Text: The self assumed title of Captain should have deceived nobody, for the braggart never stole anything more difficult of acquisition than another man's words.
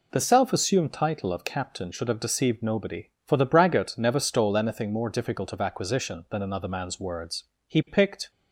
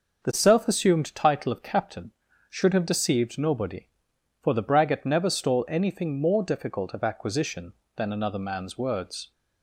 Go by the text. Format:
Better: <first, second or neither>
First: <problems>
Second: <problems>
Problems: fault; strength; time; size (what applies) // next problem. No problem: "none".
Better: second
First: goes on to say "He picked"; noticeable; from 7.6 s on; 0.62 s long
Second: none